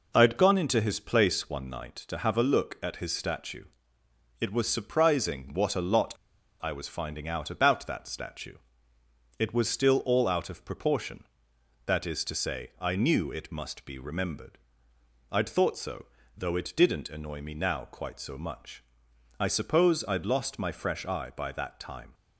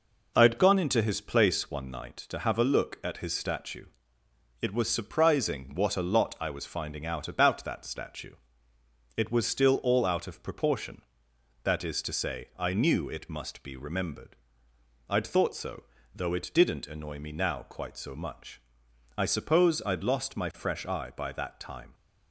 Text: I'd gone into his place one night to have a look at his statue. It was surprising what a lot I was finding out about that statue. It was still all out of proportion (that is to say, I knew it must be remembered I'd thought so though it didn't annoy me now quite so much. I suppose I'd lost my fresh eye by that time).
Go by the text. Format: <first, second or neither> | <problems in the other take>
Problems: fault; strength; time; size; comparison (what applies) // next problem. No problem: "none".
second | pauses between "lot" and "I"; noticeable; at 6.1 s; 0.49 s long // pauses between "remembered" and "I'd"; noticeable; at 14.5 s; 0.72 s long; noticeable in the second // pauses between "so" and "though"; slight; at 16.0 s; 0.32 s long; slight in the second